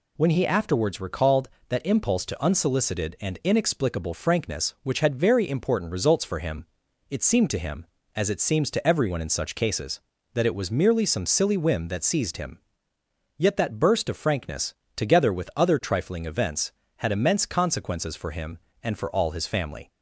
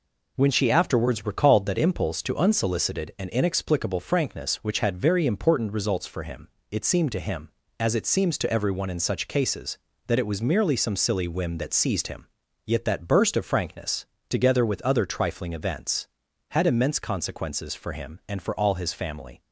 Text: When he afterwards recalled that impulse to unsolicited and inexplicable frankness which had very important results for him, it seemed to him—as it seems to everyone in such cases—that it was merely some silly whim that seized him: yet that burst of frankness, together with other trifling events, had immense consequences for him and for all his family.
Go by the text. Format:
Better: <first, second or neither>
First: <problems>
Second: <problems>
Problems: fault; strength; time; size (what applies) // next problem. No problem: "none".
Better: first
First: none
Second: says "she" for "he"; at 0.5 s